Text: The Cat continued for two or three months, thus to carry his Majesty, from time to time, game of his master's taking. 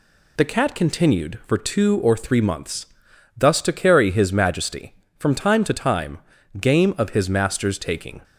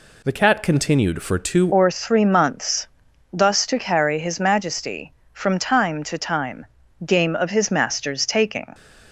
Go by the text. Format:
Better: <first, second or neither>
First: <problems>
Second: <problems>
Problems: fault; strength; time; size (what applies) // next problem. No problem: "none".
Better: first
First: none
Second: changes voice at "or"; from 1.7 s on; 7.0 s long